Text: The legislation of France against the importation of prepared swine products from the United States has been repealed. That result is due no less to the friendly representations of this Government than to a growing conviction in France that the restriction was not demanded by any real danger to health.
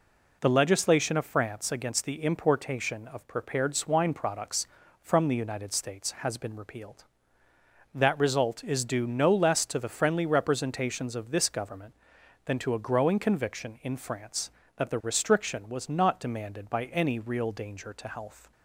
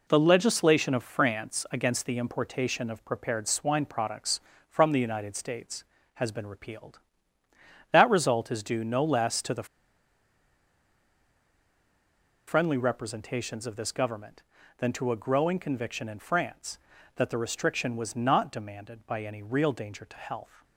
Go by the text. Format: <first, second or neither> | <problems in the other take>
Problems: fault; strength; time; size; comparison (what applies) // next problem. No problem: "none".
first | pauses between "the" and "friendly"; strong; at 9.6 s; 2.8 s long